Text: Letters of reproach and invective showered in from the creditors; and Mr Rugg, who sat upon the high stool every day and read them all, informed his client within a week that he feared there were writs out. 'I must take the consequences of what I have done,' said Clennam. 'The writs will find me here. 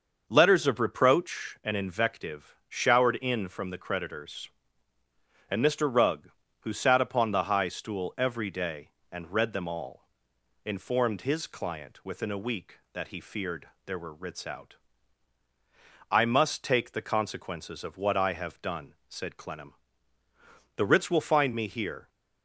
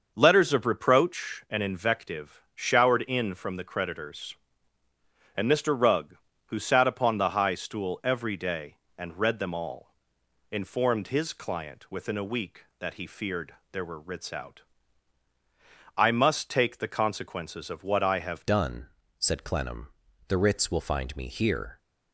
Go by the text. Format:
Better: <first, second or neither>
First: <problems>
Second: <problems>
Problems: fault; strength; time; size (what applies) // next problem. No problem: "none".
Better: first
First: starts louder than the rest; until 1.2 s; 6.5 dB // pauses between "feared" and "there"; slight; at 13.6 s; 0.16 s long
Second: starts louder than the rest; until 1.1 s; 6.5 dB // pauses between "feared" and "there"; slight; at 13.5 s; 0.16 s long // changes voice at "done"; from 18.4 s on; 3.3 s long